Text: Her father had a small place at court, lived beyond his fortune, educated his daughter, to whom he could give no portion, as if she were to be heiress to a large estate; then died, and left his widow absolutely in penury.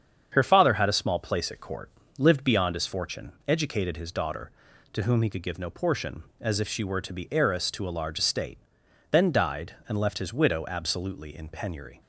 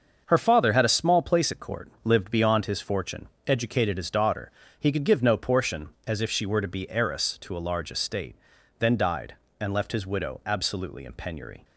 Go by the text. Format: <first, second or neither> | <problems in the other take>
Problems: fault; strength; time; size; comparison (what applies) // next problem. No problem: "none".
first | starts louder than the rest; until 1.2 s; 7 dB; strong in the first // skips "to whom"; at 4.6 s